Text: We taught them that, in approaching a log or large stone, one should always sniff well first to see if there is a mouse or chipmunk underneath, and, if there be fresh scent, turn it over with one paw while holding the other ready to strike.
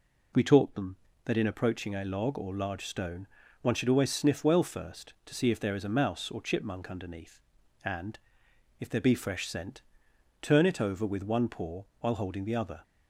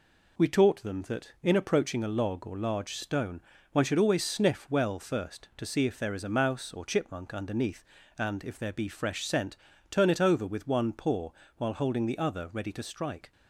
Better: second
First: pauses between "paw" and "while"; slight; at 11.8 s; 0.18 s long // stops before "ready to strike"; at 12.8 s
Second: pauses between "paw" and "while"; slight; at 11.2 s; 0.28 s long

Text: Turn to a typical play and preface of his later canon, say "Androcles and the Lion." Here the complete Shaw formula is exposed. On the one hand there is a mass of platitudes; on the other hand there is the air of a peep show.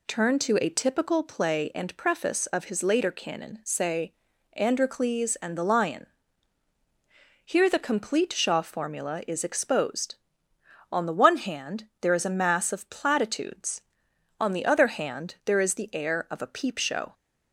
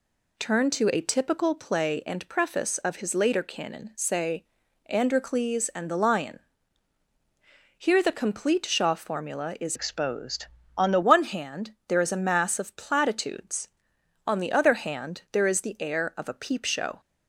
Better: first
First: pauses between "say" and "Androcles"; at 4.1 s; 0.40 s long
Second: pauses between "say" and "Androcles"; at 4.4 s; 0.42 s long // changes voice from "exposed" to "the"; from 9.7 to 11.0 s; 1.3 s long

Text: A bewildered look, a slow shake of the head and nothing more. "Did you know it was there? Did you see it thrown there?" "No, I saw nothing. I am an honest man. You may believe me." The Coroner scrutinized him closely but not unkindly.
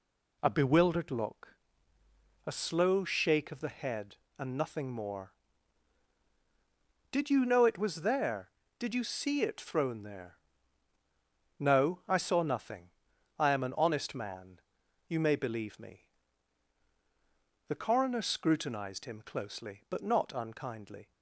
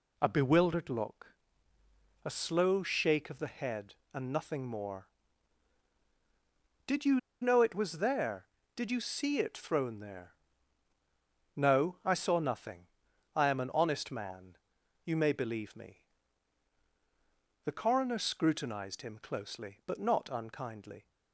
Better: first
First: none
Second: pauses between "you" and "know"; slight; at 7.1 s; 0.22 s long

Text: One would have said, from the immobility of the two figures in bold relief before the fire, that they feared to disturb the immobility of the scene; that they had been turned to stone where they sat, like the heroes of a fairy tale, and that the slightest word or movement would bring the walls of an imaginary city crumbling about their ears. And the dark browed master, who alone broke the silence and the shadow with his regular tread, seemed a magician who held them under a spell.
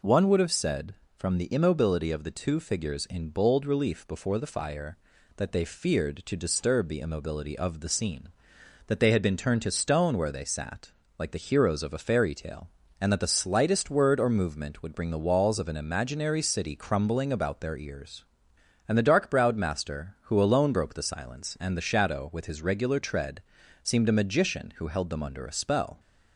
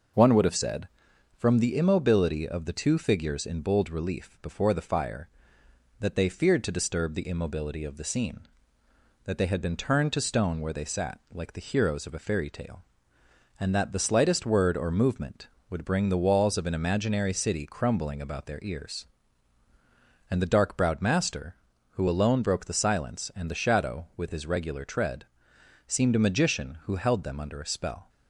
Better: neither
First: none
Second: none

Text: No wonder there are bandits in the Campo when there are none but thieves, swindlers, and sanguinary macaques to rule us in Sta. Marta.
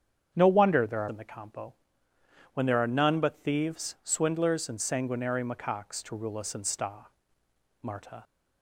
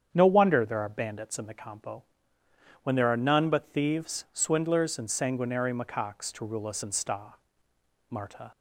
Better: second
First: starts louder than the rest; strong; until 1.3 s; 8 dB // skips "bandits"; at 1.0 s // pauses between "Campo" and "when"; noticeable; at 1.7 s; 0.80 s long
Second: starts louder than the rest; strong; until 1.1 s; 8 dB // pauses between "Campo" and "when"; noticeable; at 2.0 s; 0.80 s long

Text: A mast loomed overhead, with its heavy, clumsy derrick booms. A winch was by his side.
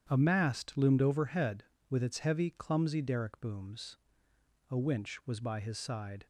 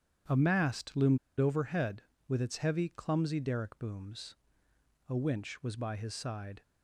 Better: first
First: starts louder than the rest; strong; until 1.1 s; 9 dB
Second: starts louder than the rest; strong; until 1.5 s; 9 dB // pauses between "loomed" and "overhead"; slight; at 1.1 s; 0.21 s long

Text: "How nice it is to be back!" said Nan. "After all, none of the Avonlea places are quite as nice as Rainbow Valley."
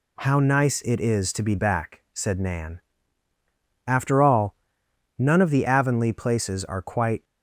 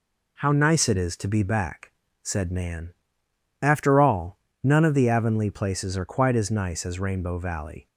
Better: second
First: stops before "as nice as Rainbow Valley"; at 7.2 s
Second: none

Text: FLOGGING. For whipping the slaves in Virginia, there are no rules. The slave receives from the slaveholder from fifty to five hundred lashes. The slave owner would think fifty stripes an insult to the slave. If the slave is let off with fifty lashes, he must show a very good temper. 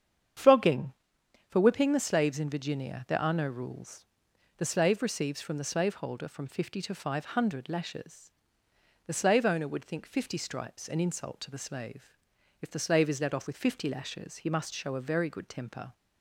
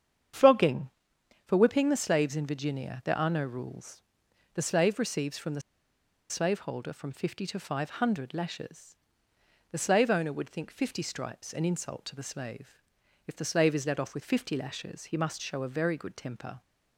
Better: first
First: starts louder than the rest; strong; until 1.9 s; 8 dB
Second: starts louder than the rest; strong; until 1.9 s; 8 dB // pauses between "the" and "slaveholder"; noticeable; at 5.6 s; 0.69 s long

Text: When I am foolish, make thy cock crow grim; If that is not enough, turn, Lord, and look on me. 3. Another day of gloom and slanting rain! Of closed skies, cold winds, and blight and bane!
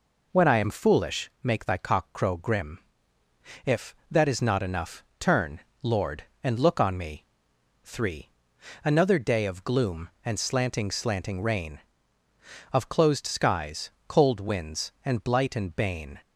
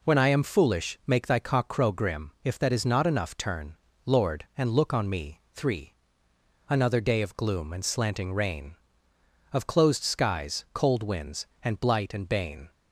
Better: second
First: says "slanting" twice; at 10.8 s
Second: none

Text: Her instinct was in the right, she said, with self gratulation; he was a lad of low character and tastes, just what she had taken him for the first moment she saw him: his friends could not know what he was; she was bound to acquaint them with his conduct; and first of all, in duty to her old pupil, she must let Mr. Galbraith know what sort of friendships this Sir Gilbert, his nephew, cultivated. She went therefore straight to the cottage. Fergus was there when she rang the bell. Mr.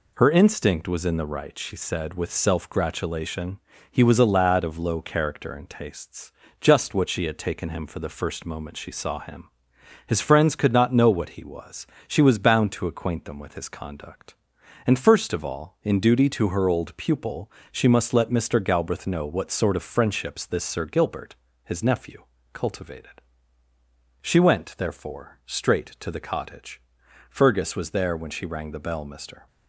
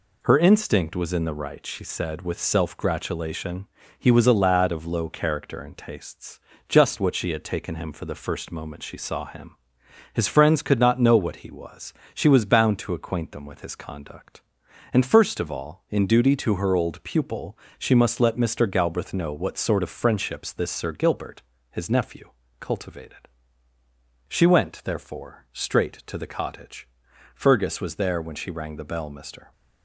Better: neither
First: none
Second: none

